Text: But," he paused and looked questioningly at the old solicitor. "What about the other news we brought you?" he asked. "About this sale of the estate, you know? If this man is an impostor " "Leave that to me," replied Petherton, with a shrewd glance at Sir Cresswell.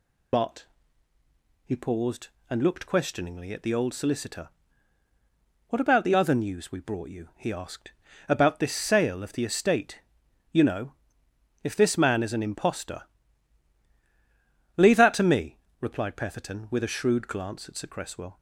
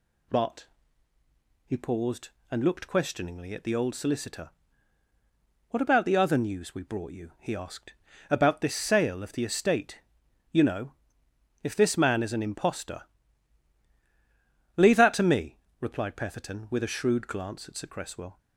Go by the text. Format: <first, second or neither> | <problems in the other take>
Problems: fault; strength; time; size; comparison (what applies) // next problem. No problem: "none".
second | loses the start of "But"; at 0.3 s; 40 ms